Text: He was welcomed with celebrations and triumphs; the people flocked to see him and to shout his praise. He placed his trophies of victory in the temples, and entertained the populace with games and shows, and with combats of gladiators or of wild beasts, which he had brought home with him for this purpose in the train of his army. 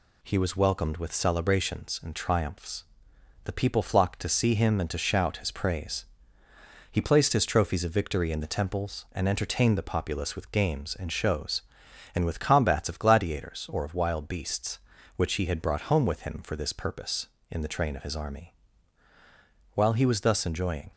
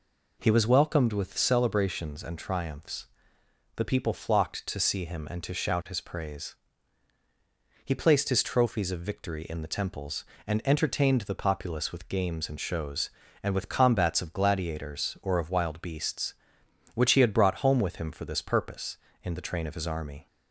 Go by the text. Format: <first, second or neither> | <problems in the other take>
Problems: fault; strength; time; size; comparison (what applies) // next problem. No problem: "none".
second | goes on to say "While he was thus enjoying"; noticeable; from 19.7 s on; 1.1 s long